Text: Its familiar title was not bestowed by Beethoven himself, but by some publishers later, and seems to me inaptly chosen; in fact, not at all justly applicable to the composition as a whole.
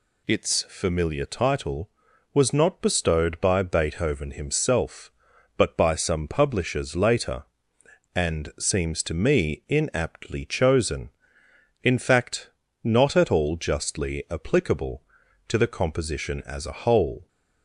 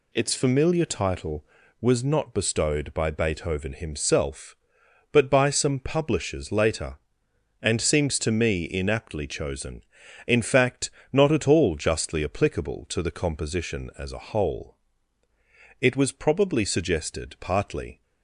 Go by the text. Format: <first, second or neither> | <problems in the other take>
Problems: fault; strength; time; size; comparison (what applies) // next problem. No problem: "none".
first | goes on to say "It was probably suggested partly"; strong; from 15.7 s on; 2.2 s long